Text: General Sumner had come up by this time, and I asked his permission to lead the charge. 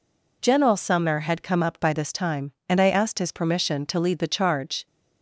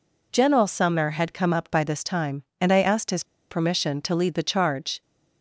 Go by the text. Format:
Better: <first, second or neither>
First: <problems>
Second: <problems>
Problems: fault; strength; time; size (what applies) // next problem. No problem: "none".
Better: first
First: none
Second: pauses between "his" and "permission"; slight; at 3.2 s; 0.26 s long